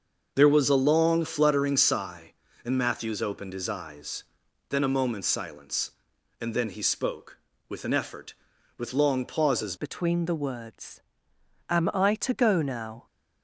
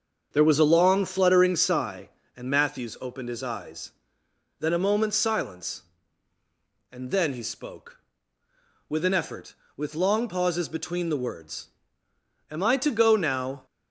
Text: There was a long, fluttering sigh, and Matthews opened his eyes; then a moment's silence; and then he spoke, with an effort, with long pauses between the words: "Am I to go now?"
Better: second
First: starts louder than the rest; until 1.3 s; 6.5 dB // changes voice at "between"; from 9.7 s on; 3.3 s long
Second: starts louder than the rest; until 1.3 s; 6.5 dB

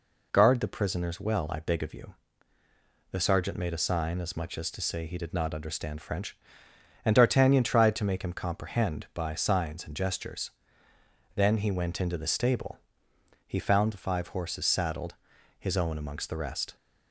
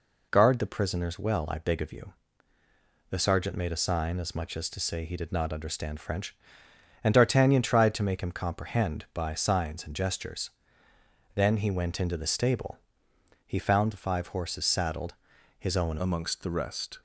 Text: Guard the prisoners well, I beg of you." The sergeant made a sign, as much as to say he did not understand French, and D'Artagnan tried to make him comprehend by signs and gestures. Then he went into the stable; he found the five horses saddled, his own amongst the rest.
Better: first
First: none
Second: changes voice at "amongst"; from 15.9 s on; 1.1 s long

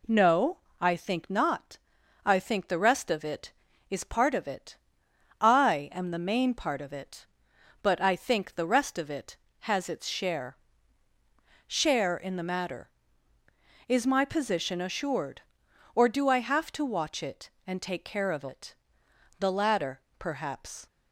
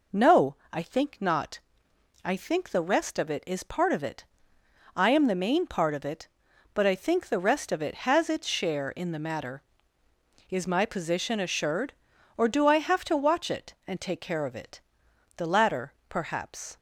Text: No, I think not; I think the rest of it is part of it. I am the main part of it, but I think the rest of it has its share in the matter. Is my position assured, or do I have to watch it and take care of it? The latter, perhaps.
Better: second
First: says "share" twice; at 11.6 s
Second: none

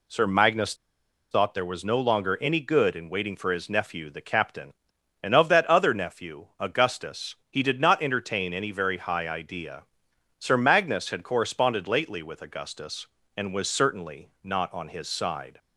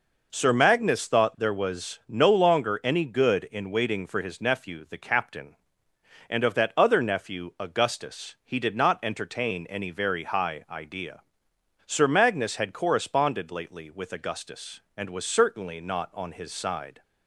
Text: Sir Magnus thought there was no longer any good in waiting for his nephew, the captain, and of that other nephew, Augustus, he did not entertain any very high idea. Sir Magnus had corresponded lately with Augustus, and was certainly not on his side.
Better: second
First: pauses between "Magnus" and "thought"; noticeable; at 0.7 s; 0.57 s long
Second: none

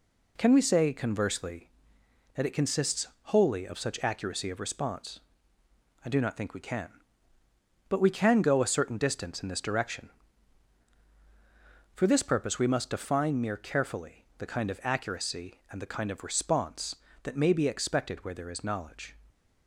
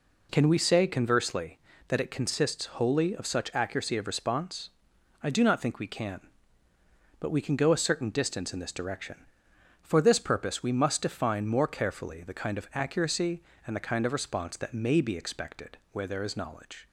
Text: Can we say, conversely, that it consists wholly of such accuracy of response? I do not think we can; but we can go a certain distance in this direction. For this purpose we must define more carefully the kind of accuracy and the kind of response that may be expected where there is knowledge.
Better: second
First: pauses between "consists" and "wholly"; slight; at 3.0 s; 0.16 s long // says "mere" for "more"; at 13.4 s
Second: none

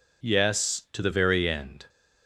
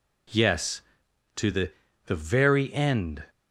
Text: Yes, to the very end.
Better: first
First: none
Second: says "the" twice; at 2.0 s

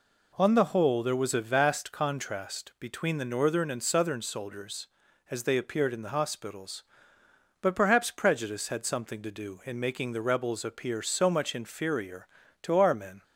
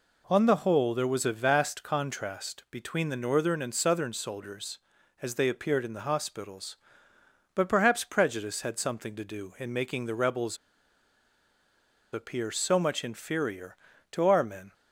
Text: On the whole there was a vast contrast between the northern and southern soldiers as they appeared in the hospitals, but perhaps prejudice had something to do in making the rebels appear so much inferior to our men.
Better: first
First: none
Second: pauses between "rebels" and "appear"; strong; at 10.5 s; 1.5 s long

